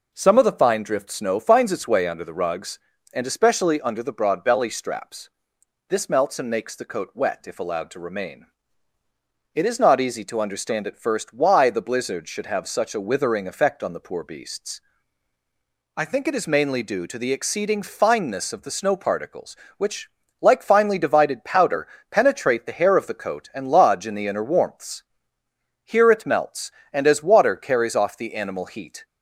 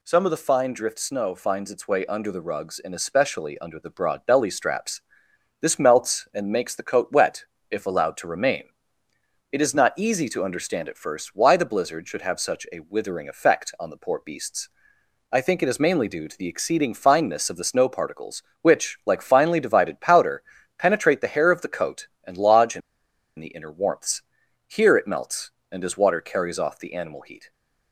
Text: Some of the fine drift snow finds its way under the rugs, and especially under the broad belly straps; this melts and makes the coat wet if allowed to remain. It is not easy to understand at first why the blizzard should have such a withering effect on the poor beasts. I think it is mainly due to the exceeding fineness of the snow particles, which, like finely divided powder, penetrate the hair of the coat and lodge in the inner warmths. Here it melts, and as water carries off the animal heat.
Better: first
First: none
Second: pauses between "wet" and "if"; slight; at 7.4 s; 0.26 s long // pauses between "in" and "the"; noticeable; at 22.8 s; 0.58 s long

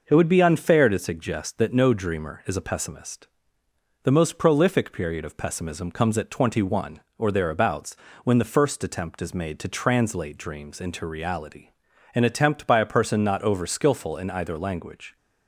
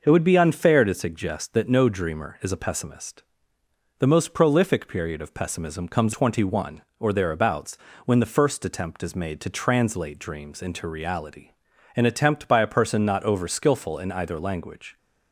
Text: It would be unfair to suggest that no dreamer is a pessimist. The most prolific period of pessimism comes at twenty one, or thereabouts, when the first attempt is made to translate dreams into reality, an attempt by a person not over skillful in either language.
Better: first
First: none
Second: skips "at"; at 6.1 s

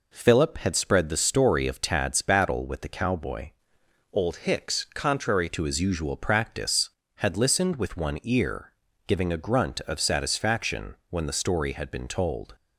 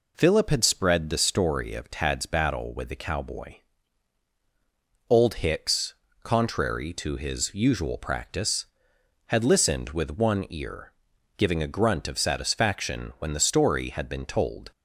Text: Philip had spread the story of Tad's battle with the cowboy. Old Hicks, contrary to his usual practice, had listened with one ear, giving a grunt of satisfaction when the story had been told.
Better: second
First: changes voice from "Old" to "contrary"; from 4.1 to 5.4 s; 1.3 s long // pauses between "satisfaction" and "when"; slight; at 10.9 s; 0.16 s long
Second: none

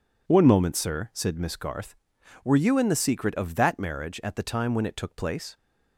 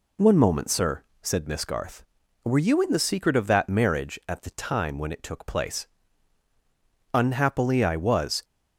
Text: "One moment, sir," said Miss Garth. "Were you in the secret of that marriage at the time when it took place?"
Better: first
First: none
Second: goes on to say "Unhappily I was"; noticeable; from 7.1 s on; 1.3 s long

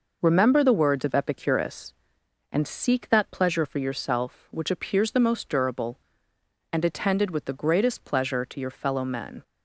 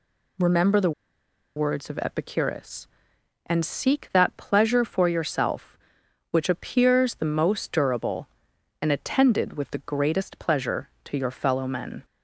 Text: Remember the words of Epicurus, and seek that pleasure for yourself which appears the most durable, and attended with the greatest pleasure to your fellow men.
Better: first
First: none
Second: pauses between "the" and "words"; noticeable; at 0.9 s; 0.65 s long

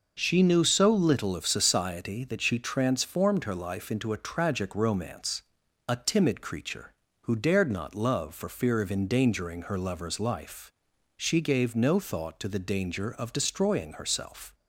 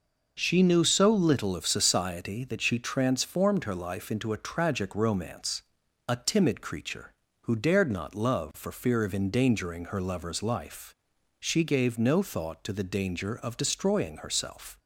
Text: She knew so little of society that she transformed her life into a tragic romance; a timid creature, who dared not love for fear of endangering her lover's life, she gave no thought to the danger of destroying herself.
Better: neither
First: none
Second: none

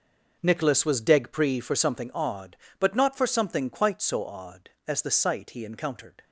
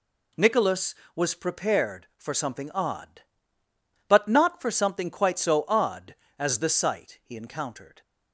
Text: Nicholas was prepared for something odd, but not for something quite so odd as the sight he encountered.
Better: second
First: says "degpree" for "prepared"; at 1.0 s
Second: none

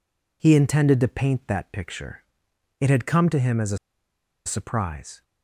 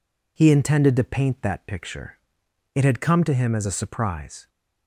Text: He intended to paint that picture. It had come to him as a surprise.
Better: second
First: pauses between "a" and "surprise"; noticeable; at 3.7 s; 0.68 s long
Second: none

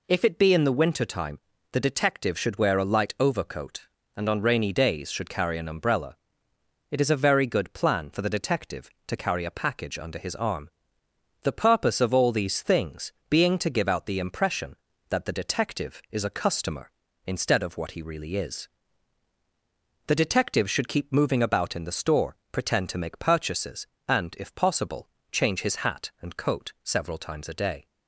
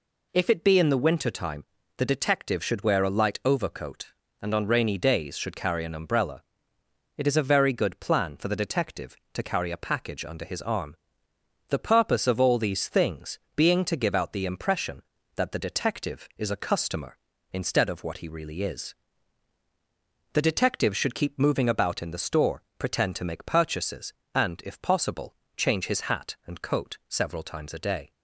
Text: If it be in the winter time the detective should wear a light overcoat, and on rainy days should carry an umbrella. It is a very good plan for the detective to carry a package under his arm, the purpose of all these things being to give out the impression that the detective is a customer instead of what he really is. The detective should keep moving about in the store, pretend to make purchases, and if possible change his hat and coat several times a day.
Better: neither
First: pauses between "time" and "the"; slight; at 1.3 s; 0.32 s long // pauses between "things" and "being"; slight; at 13.1 s; 0.20 s long // pauses between "possible" and "change"; slight; at 25.0 s; 0.24 s long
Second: pauses between "time" and "the"; slight; at 1.6 s; 0.32 s long // pauses between "things" and "being"; slight; at 13.3 s; 0.20 s long // pauses between "possible" and "change"; slight; at 25.3 s; 0.22 s long

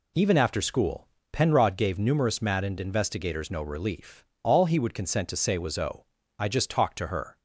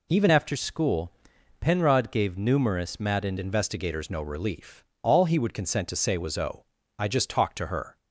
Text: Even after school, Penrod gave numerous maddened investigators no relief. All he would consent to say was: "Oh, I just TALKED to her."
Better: first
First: none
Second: changes voice from "after" to "maddened"; from 0.3 to 3.3 s; 3.0 s long

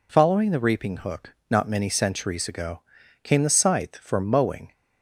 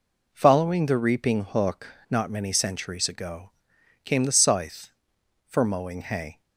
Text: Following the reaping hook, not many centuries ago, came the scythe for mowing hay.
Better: second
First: stops before "hay"; at 4.7 s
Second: none

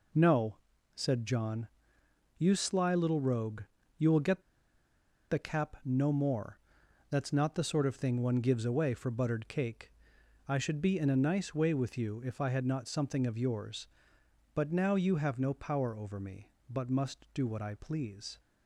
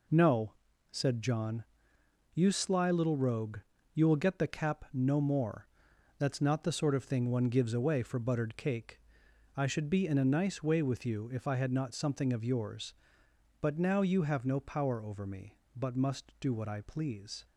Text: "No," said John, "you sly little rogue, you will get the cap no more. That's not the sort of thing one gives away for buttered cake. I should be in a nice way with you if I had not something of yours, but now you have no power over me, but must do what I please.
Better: second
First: pauses between "get" and "the"; noticeable; at 4.4 s; 0.88 s long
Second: none

